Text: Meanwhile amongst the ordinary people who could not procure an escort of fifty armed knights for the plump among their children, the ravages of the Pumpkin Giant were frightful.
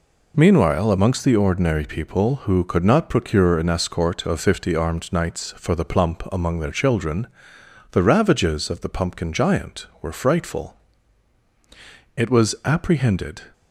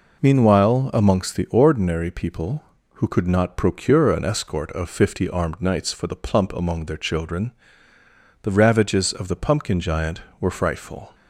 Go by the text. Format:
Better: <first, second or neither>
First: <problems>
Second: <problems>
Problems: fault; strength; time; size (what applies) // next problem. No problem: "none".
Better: second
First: goes on to say "It was apprehended"; noticeable; from 12.1 s on; 1.2 s long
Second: none